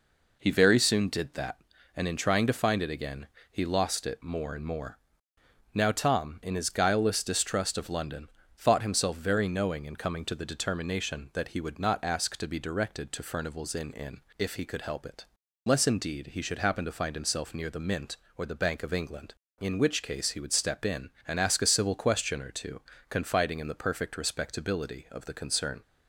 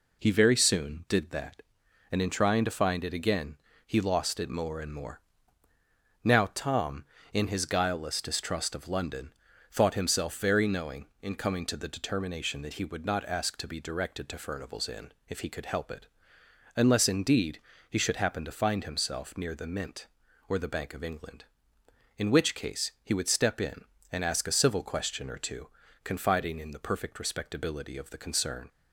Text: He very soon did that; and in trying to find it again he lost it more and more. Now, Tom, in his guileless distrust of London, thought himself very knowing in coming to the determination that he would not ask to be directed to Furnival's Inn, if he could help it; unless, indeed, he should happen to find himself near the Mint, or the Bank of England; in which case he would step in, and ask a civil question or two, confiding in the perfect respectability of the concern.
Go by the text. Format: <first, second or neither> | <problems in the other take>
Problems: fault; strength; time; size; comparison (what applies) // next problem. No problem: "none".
second | pauses between "again" and "he"; slight; at 3.2 s; 0.24 s long; slight in the second // says "Inn" twice; at 13.9 s